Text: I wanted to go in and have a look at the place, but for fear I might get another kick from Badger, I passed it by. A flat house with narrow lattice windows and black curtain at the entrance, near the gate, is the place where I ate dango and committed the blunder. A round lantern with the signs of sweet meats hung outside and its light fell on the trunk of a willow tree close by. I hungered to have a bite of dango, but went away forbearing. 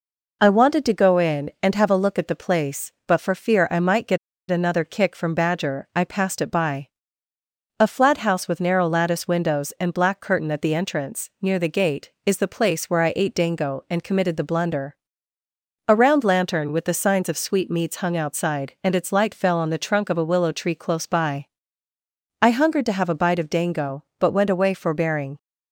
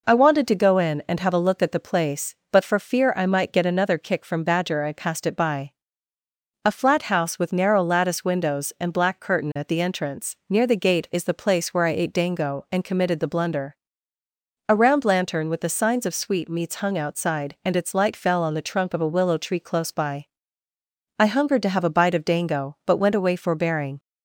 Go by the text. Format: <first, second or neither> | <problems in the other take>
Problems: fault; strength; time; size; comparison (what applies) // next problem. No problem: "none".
second | pauses between "get" and "another"; slight; at 4.1 s; 0.31 s long